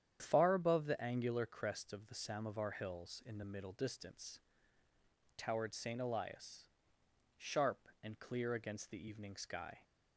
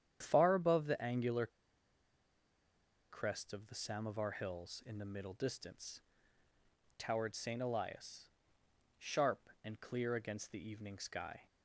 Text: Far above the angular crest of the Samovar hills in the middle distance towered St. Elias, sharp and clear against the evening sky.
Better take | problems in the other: first | starts louder than the rest; strong; until 1.2 s; 9 dB; strong in the first // pauses between "angular" and "crest"; strong; at 1.4 s; 1.6 s long // pauses between "distance" and "towered"; at 5.9 s; 1.0 s long; also in the first

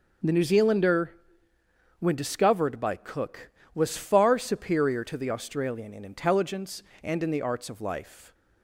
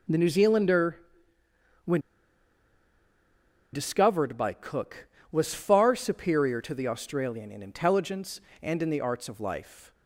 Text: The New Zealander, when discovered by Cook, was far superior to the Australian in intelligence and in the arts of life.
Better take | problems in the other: first | pauses between "when" and "discovered"; strong; at 1.9 s; 1.7 s long

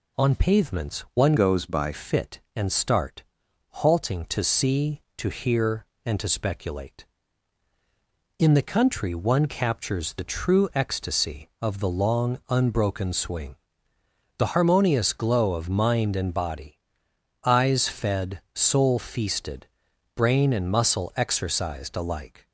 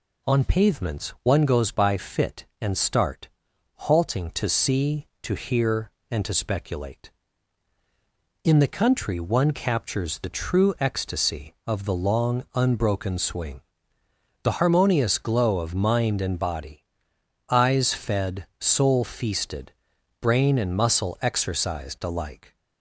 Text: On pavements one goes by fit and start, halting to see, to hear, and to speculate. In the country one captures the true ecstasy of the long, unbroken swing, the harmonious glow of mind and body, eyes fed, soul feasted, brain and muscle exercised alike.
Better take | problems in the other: second | changes voice from "goes" to "by"; from 1.3 to 1.9 s; 0.6 s long

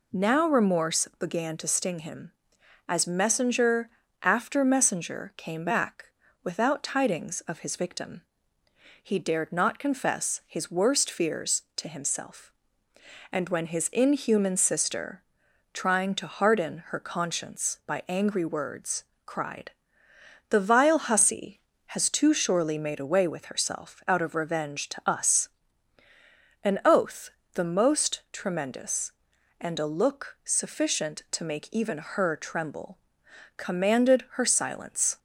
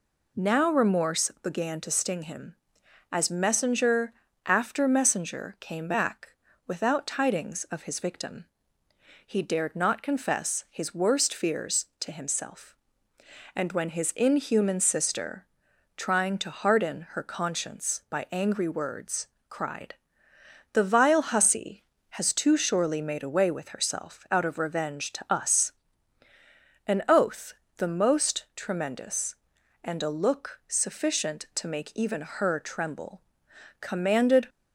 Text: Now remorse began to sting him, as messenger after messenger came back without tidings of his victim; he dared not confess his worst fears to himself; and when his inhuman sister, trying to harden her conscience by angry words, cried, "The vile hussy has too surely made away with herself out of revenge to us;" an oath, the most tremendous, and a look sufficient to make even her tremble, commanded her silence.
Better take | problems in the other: first | pauses between "messenger" and "after"; slight; at 4.1 s; 0.34 s long; slight in the first // pauses between "back" and "without"; slight; at 6.2 s; 0.36 s long; slight in the first // stops before "her silence"; at 34.4 s

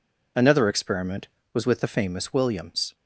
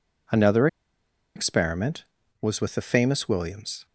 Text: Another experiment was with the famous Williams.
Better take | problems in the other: first | pauses between "Another" and "experiment"; noticeable; at 0.6 s; 0.68 s long

